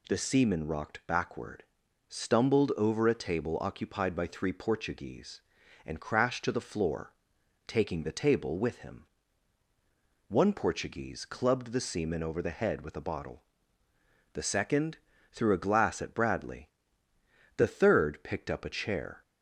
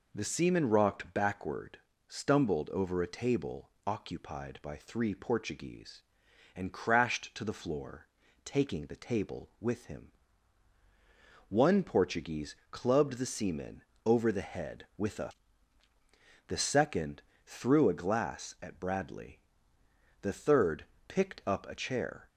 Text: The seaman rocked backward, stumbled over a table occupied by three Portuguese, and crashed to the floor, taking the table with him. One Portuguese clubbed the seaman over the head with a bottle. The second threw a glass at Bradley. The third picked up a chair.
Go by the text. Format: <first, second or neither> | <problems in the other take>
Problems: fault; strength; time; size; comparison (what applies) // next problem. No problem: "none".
first | pauses between "table" and "occupied"; slight; at 3.6 s; 0.16 s long // pauses between "Portuguese" and "clubbed"; slight; at 12.5 s; 0.16 s long // pauses between "seaman" and "over"; slight; at 13.8 s; 0.20 s long // skips "bottle"; at 15.8 s // pauses between "second" and "threw"; slight; at 17.2 s; 0.24 s long; slight in the first // pauses between "third" and "picked"; slight; at 20.8 s; 0.24 s long